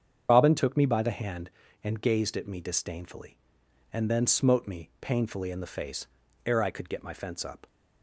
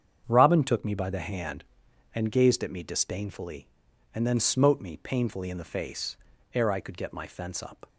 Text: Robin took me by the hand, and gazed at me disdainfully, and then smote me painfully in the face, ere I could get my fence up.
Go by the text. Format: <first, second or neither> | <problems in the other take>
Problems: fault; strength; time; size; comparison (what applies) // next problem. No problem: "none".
second | loses the start of "Robin"; at 0.2 s; 90 ms // starts louder than the rest; strong; until 1.3 s; 7.5 dB; strong in the second